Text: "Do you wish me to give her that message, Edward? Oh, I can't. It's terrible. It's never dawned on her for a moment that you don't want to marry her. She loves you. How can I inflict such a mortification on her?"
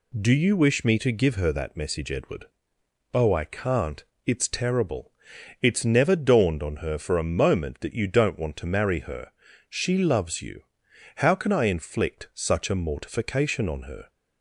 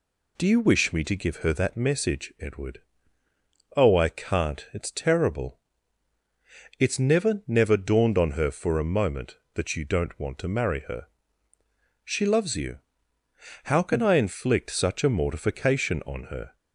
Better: first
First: none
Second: says "never" twice; at 7.4 s

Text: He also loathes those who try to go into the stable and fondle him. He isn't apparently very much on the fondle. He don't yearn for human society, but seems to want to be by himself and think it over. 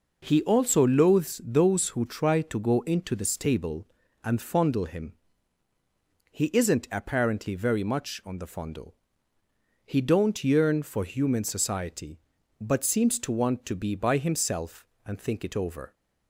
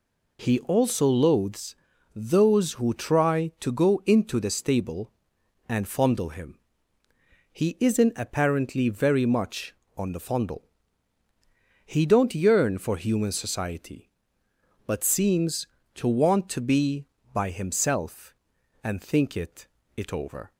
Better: first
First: none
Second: pauses between "loathes" and "those"; at 1.7 s; 0.40 s long // says "it" twice; at 19.9 s

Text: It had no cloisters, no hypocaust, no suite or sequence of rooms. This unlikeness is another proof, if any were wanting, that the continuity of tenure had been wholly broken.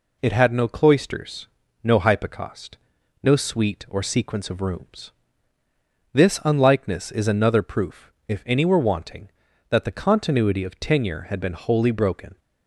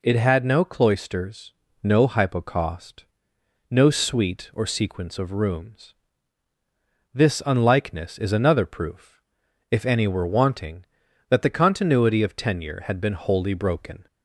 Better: neither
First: none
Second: none

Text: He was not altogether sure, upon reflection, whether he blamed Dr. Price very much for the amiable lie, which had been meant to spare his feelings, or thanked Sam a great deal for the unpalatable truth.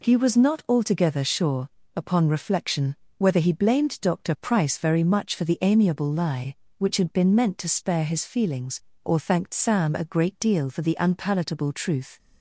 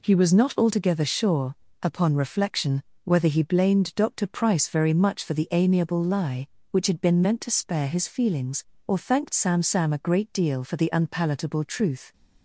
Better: first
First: none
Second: says "Sam" twice; at 9.6 s

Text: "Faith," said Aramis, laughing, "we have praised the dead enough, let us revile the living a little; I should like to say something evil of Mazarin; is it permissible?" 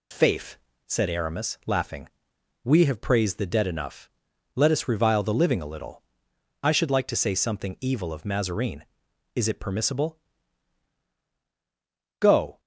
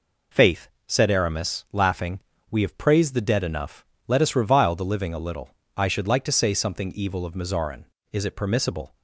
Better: second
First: goes on to say "Go"; slight; from 12.1 s on; 0.40 s long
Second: none

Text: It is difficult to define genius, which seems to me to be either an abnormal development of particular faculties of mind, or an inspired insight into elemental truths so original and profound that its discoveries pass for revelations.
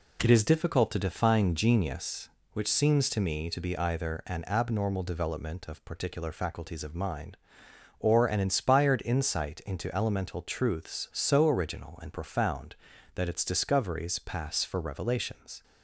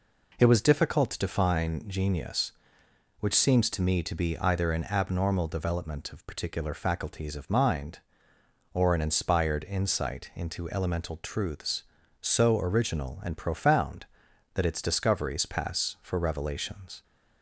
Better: first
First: none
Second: says "was" for "is"; at 0.4 s

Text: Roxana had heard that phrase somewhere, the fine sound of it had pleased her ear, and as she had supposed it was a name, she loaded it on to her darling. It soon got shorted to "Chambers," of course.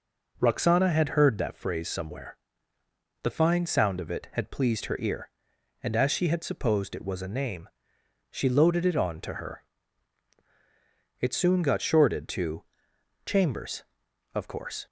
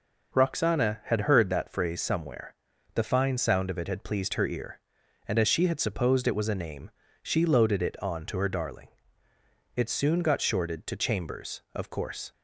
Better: second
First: skips "darling"; at 10.4 s // pauses between "to" and "Chambers"; noticeable; at 12.6 s; 0.62 s long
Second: none

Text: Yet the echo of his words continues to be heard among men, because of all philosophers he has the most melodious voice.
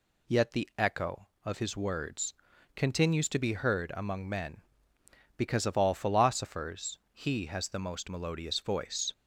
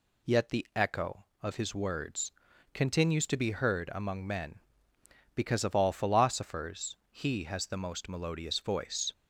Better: neither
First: pauses between "words" and "continues"; at 2.3 s; 0.42 s long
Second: pauses between "words" and "continues"; at 2.3 s; 0.42 s long

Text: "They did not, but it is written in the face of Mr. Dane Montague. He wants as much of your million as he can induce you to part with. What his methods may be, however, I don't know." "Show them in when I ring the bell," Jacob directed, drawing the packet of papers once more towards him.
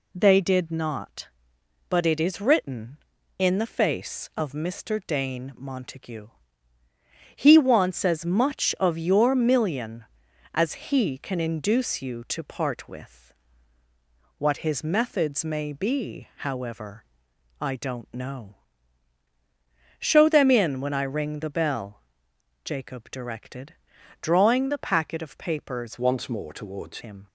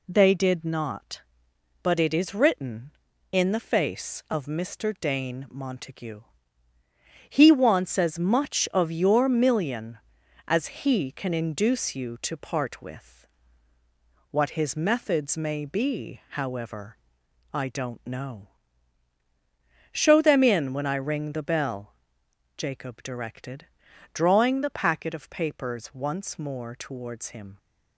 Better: second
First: changes voice from "once" to "towards"; from 25.9 to 26.9 s; 1.0 s long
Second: none

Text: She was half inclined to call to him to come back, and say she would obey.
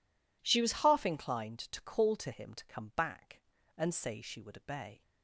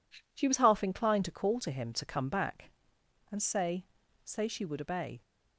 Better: first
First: none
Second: says "say" twice; at 4.2 s

